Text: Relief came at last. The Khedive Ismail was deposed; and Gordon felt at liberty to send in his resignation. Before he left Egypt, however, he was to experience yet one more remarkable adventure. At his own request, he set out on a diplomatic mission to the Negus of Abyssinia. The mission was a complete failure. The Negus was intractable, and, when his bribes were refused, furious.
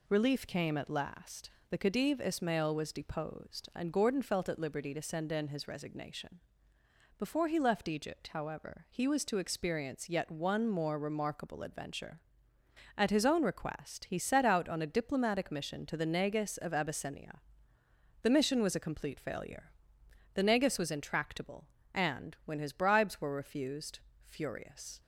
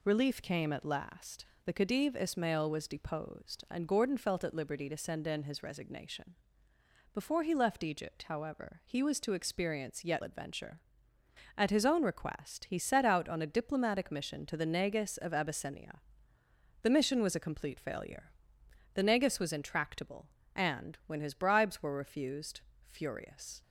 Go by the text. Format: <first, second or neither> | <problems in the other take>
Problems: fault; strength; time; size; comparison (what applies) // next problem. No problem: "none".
first | skips "one more remarkable"; at 10.2 s